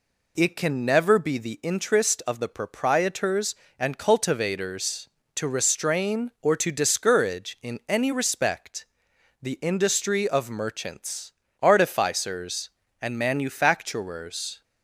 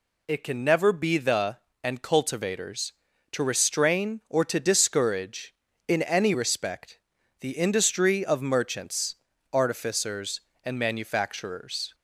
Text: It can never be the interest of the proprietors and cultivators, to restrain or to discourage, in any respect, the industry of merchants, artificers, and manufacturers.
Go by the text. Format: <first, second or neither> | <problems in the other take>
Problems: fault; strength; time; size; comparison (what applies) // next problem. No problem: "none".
first | skips "interest of the proprietors"; at 1.7 s